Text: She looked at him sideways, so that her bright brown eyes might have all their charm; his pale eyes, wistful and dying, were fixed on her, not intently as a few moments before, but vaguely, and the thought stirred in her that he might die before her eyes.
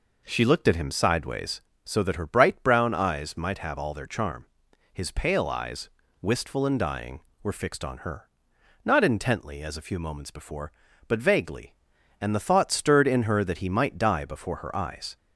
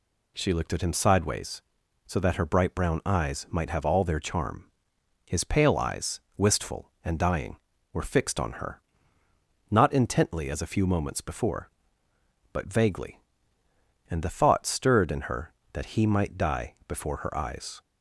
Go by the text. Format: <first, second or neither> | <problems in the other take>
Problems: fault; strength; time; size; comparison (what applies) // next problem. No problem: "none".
second | starts louder than the rest; noticeable; until 1.9 s; 4.5 dB